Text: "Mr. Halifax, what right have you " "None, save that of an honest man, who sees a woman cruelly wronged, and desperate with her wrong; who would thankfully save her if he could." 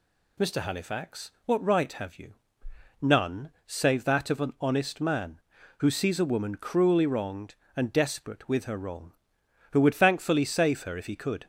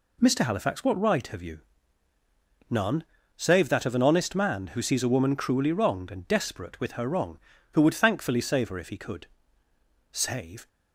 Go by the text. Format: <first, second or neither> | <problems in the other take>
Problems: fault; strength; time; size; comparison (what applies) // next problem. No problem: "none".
first | goes on to say "Save"; from 10.1 s on; 0.56 s long